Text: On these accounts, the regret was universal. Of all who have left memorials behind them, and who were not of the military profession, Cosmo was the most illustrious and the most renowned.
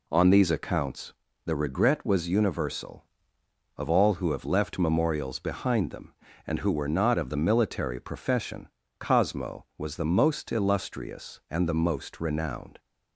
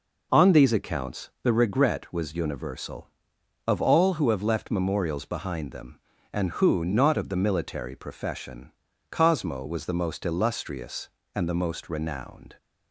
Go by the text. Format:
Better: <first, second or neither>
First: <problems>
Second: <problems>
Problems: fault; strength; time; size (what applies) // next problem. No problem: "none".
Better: first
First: none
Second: skips "were"; at 6.8 s